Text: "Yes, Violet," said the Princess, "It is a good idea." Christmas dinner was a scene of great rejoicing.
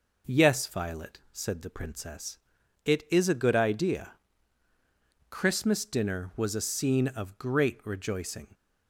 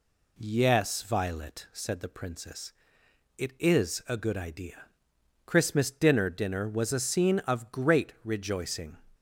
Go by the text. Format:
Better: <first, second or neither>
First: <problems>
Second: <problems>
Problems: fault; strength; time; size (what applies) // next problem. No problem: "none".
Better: first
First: none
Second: says "dinner" twice; at 6.2 s